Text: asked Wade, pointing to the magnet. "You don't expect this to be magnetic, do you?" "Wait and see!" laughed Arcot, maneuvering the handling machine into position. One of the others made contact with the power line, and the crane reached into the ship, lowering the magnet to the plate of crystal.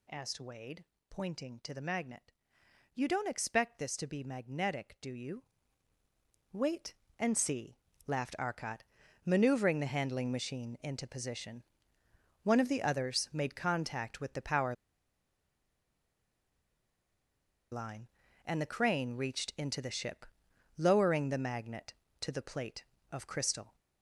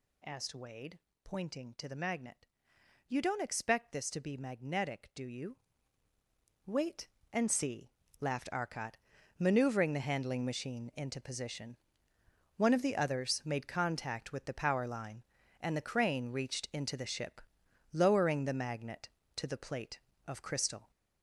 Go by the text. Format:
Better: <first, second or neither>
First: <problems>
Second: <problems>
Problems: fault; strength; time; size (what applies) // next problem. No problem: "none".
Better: second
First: pauses between "power" and "line"; strong; at 14.7 s; 2.9 s long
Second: none